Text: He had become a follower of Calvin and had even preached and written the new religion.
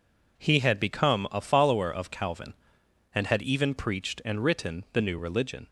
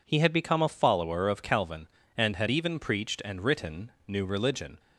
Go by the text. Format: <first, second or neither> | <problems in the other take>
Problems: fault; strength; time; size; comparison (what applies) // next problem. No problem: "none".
first | skips "the"; at 3.9 s